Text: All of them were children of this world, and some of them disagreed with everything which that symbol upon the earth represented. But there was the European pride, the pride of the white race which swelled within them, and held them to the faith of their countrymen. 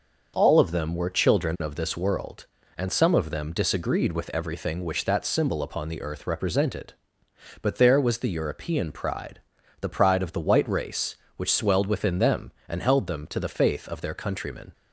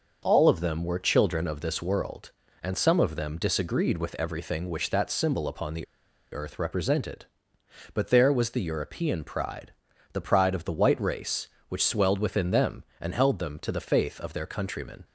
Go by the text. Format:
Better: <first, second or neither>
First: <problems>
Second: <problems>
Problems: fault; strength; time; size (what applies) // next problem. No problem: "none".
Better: first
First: none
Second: pauses between "the" and "earth"; noticeable; at 5.8 s; 0.47 s long